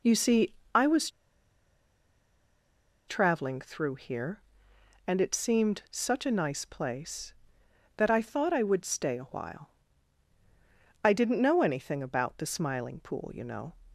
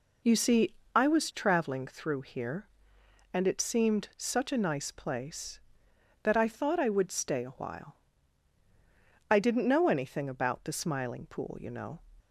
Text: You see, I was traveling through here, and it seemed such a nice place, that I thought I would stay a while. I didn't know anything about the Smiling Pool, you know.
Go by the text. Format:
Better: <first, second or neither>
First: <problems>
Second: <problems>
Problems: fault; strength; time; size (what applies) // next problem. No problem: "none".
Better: second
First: pauses between "was" and "traveling"; strong; at 1.0 s; 1.9 s long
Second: none